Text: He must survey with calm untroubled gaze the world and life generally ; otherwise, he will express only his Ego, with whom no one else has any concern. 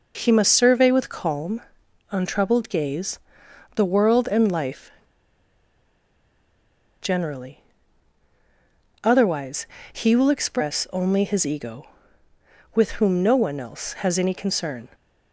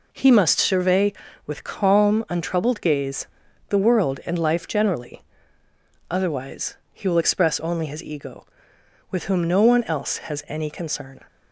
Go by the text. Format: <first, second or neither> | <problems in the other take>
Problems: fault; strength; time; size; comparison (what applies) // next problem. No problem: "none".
second | pauses between "calm" and "untroubled"; noticeable; at 1.5 s; 0.50 s long // pauses between "gaze" and "the"; noticeable; at 3.1 s; 0.56 s long; also in the second // pauses between "life" and "generally"; strong; at 4.8 s; 2.1 s long